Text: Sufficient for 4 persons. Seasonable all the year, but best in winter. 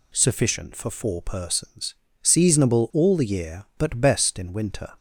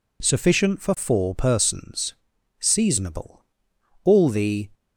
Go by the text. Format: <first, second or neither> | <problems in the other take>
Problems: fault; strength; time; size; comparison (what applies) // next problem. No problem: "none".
first | pauses between "Seasonable" and "all"; noticeable; at 3.4 s; 0.64 s long // stops before "year but best in winter"; at 4.7 s